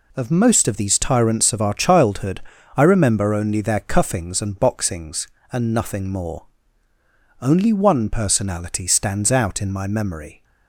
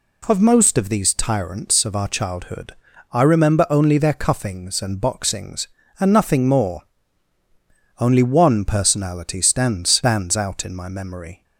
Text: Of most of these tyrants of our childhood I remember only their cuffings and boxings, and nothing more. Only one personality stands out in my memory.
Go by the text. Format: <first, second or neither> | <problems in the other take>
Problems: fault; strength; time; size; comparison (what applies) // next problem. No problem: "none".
first | pauses between "childhood" and "I"; at 2.7 s; 0.38 s long; slight in the first // says "stands" twice; at 9.8 s